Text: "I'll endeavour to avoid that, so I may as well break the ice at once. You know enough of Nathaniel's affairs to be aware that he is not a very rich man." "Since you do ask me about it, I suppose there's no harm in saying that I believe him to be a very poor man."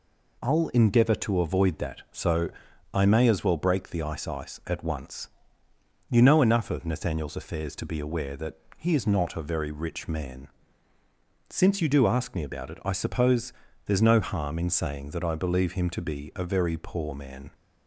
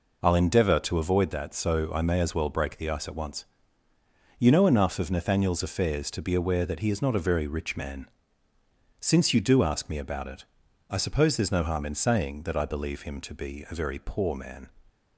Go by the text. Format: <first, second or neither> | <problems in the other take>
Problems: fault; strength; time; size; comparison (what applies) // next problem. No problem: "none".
second | pauses between "so" and "I"; at 2.4 s; 0.44 s long // says "ice" twice; at 4.2 s // pauses between "that" and "he"; slight; at 8.5 s; 0.20 s long // pauses between "suppose" and "there's"; slight; at 13.5 s; 0.34 s long